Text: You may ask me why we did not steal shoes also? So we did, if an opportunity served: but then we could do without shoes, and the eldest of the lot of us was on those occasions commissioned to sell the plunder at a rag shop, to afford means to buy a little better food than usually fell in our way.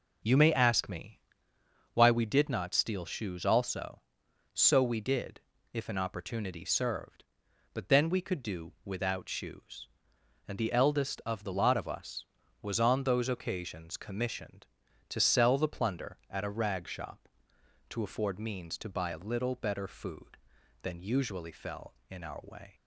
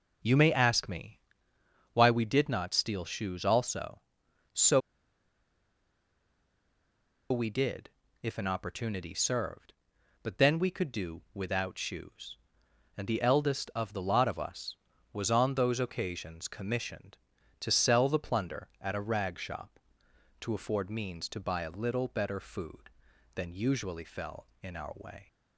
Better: first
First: pauses between "me" and "why"; noticeable; at 1.1 s; 0.76 s long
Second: pauses between "me" and "why"; noticeable; at 1.1 s; 0.76 s long // pauses between "So" and "we"; strong; at 4.7 s; 2.5 s long

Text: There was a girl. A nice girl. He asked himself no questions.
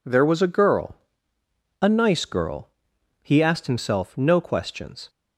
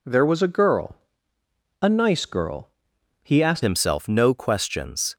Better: first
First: none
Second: changes voice at "himself"; from 3.6 s on; 1.5 s long

